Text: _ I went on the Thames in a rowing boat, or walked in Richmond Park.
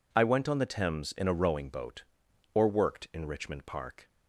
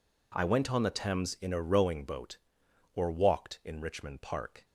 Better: second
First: says "worked" for "walked"; at 2.6 s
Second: none

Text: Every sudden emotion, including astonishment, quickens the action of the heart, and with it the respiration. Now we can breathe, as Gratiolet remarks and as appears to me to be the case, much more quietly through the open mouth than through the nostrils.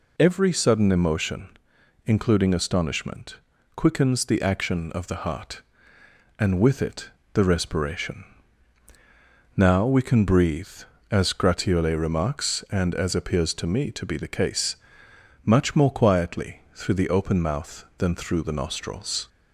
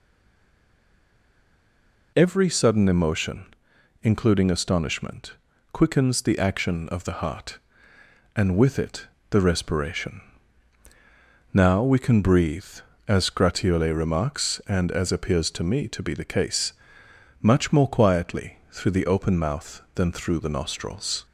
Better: first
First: pauses between "it" and "the"; slight; at 7.0 s; 0.24 s long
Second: stays silent before the first word; until 2.1 s; 2.1 s long // pauses between "it" and "the"; slight; at 9.0 s; 0.24 s long

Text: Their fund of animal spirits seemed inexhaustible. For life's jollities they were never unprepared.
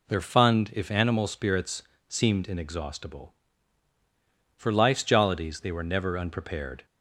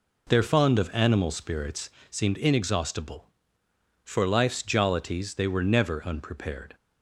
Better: second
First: says "if" for "of"; at 0.7 s // pauses between "spirits" and "seemed"; slight; at 1.8 s; 0.26 s long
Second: pauses between "spirits" and "seemed"; slight; at 1.8 s; 0.22 s long

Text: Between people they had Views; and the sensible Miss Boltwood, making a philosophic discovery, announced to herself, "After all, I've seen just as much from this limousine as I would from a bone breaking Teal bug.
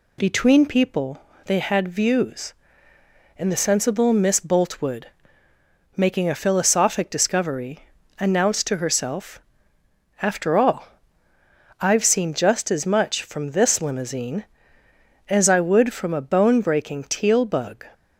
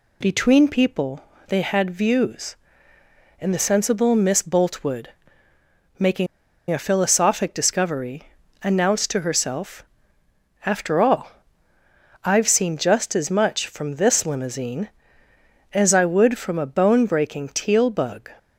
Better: first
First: pauses between "people" and "they"; slight; at 1.2 s; 0.24 s long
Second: pauses between "people" and "they"; slight; at 1.2 s; 0.24 s long // pauses between "making" and "a"; at 6.2 s; 0.44 s long

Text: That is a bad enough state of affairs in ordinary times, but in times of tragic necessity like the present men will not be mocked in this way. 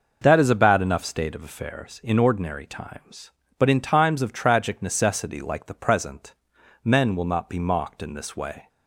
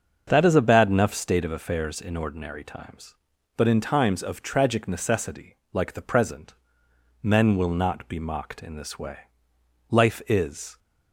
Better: first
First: pauses between "present" and "men"; noticeable; at 6.3 s; 0.52 s long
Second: starts louder than the rest; until 1.2 s; 6.5 dB // pauses between "necessity" and "like"; slight; at 5.5 s; 0.16 s long // pauses between "present" and "men"; noticeable; at 6.5 s; 0.70 s long // goes on to say "Life is"; noticeable; from 9.9 s on; 0.88 s long

